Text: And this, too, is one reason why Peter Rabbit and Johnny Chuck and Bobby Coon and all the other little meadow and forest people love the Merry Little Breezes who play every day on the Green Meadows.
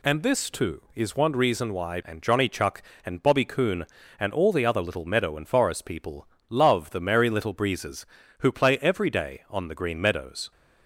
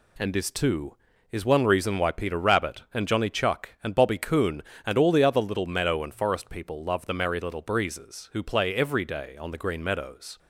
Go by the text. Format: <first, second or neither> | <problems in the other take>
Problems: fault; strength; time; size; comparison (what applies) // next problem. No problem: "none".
second | skips "Peter Rabbit"; at 2.0 s // pauses between "people" and "love"; slight; at 6.2 s; 0.22 s long